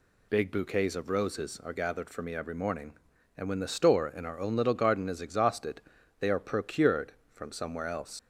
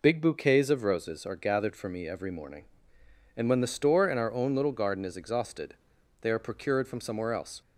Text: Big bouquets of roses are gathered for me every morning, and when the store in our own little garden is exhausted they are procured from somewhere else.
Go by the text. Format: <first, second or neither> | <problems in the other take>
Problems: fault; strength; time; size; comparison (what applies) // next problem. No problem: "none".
second | pauses between "exhausted" and "they"; slight; at 5.8 s; 0.36 s long; noticeable in the second // leaves "else" unfinished; at 8.1 s; 95 ms